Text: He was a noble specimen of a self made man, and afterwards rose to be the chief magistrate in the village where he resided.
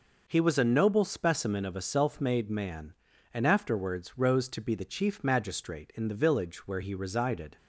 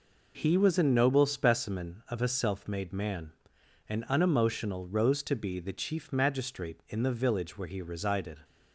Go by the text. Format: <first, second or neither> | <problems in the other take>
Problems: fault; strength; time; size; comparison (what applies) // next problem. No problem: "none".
first | says "unemotional" for "afterwards"; at 4.0 s